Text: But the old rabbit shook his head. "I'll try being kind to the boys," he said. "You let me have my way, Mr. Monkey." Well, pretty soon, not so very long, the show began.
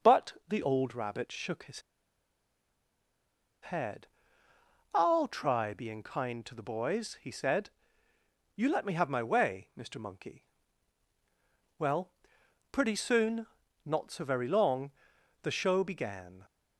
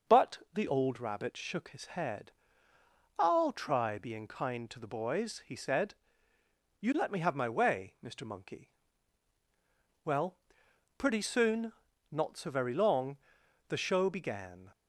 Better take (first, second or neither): second